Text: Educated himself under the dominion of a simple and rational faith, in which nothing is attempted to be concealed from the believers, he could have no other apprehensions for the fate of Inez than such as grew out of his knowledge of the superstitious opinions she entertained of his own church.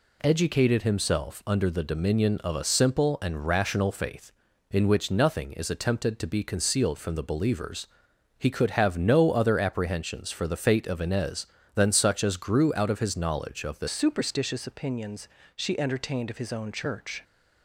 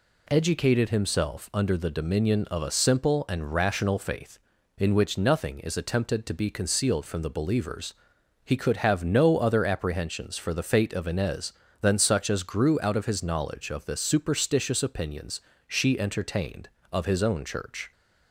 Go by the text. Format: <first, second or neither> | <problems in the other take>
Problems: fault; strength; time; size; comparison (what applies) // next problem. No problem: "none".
second | changes voice at "superstitious"; from 13.8 s on; 3.4 s long // pauses between "opinions" and "she"; slight; at 15.2 s; 0.26 s long; slight in the second